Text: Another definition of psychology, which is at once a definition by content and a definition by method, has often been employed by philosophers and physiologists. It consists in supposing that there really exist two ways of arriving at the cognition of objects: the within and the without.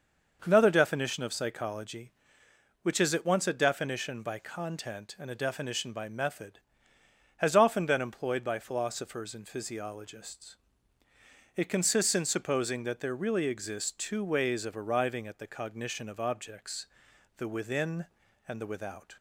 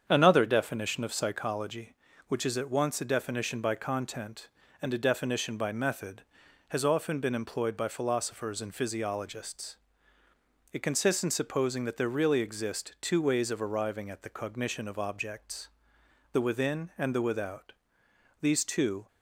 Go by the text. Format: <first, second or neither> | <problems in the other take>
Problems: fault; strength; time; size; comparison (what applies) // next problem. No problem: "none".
first | starts louder than the rest; strong; until 1.0 s; 7.5 dB; noticeable in the first // goes on to say "These two"; noticeable; from 18.4 s on; 0.66 s long